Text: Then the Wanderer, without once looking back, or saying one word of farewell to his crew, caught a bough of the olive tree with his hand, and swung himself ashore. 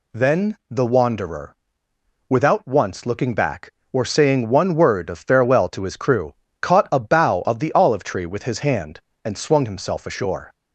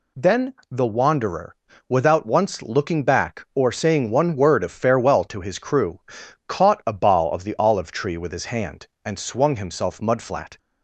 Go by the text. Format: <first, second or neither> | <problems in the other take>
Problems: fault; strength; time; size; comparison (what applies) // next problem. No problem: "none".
first | pauses between "Then" and "the"; slight; at 0.5 s; 0.18 s long // says "mudflat" for "ashore"; at 10.0 s